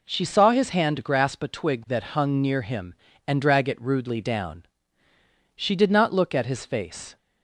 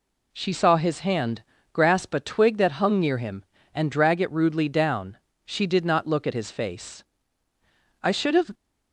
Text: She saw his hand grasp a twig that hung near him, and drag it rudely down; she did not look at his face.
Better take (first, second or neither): first